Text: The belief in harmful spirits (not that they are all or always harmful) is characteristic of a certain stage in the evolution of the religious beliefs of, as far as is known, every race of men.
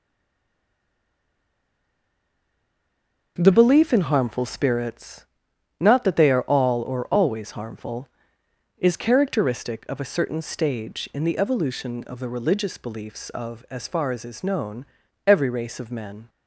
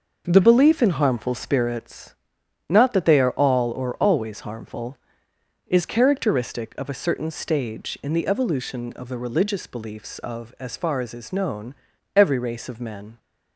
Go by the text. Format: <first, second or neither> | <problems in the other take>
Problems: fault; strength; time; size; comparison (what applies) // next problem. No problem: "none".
second | stays silent before the first word; strong; until 3.3 s; 3.3 s long // starts louder than the rest; noticeable; until 4.3 s; 6 dB; noticeable in the second